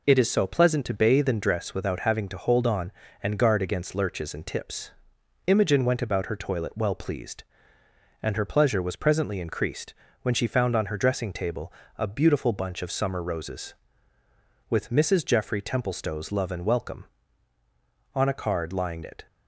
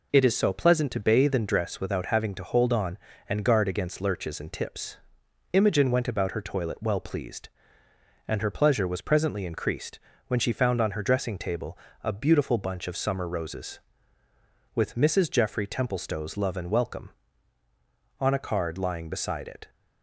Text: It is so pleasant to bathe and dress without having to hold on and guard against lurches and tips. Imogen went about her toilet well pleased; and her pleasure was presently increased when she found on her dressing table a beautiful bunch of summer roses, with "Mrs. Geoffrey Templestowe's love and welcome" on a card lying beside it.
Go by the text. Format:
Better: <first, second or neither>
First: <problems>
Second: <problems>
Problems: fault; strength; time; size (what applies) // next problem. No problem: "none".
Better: second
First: pauses between "increased" and "when"; slight; at 9.9 s; 0.28 s long // pauses between "table" and "a"; slight; at 11.7 s; 0.26 s long // skips "beside"; at 19.0 s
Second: pauses between "increased" and "when"; slight; at 9.9 s; 0.28 s long // pauses between "table" and "a"; slight; at 11.7 s; 0.26 s long